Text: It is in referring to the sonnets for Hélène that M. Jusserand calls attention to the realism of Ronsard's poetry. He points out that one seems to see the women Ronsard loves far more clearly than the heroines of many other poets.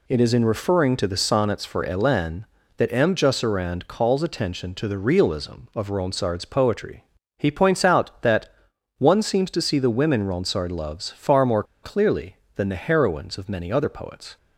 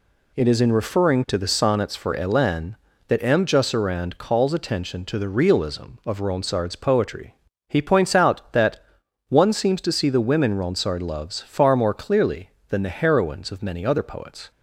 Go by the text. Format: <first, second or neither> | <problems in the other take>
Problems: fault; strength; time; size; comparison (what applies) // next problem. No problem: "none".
second | pauses between "that" and "one"; noticeable; at 8.4 s; 0.48 s long; noticeable in the second // pauses between "more" and "clearly"; slight; at 11.6 s; 0.19 s long